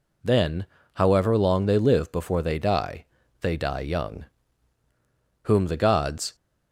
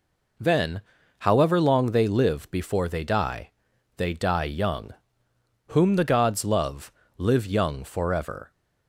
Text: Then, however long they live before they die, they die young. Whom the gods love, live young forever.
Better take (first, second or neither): second